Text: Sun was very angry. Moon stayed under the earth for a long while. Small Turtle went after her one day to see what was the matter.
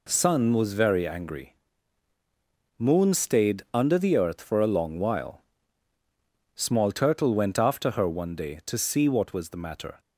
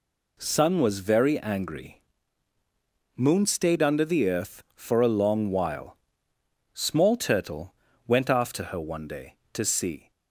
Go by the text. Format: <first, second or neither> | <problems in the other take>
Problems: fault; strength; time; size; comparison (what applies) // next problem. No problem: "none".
first | pauses between "Turtle" and "went"; slight; at 7.7 s; 0.32 s long // stops before "what was the matter"; at 10.1 s